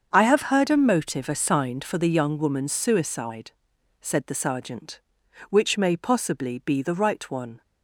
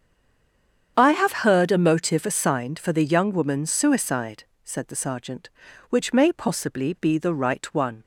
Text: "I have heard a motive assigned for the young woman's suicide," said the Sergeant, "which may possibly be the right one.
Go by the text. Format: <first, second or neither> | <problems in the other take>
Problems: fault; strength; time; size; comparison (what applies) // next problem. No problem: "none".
first | stays silent before the first word; slight; until 0.9 s; 0.9 s long // starts louder than the rest; strong; until 1.9 s; 8 dB; also in the first